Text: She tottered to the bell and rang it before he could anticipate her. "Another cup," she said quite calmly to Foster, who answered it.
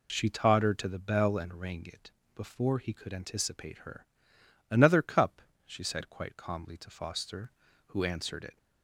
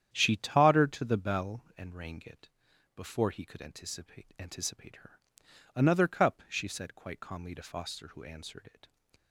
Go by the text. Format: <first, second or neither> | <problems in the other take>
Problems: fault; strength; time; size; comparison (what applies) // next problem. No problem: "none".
first | starts louder than the rest; strong; until 1.1 s; 9.5 dB // pauses between "it" and "before"; noticeable; at 2.5 s; 0.46 s long; slight in the first // says "anticipate" twice; at 4.3 s